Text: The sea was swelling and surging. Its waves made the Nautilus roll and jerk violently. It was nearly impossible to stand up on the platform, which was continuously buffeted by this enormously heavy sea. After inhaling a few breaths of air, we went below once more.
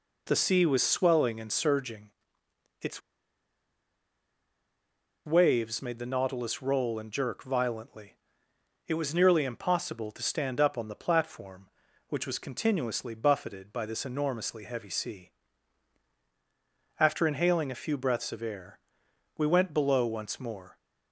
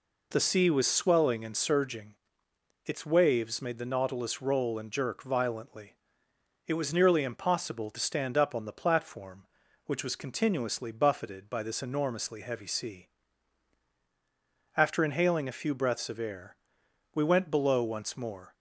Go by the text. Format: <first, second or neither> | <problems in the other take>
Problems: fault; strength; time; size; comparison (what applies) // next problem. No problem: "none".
second | pauses between "Its" and "waves"; strong; at 2.9 s; 2.2 s long